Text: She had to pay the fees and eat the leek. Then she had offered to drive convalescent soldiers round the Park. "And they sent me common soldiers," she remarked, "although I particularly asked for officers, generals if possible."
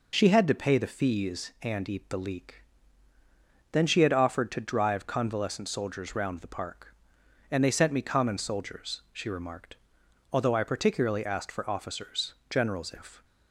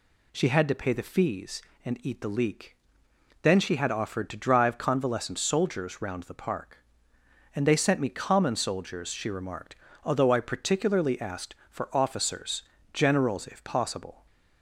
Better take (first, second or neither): second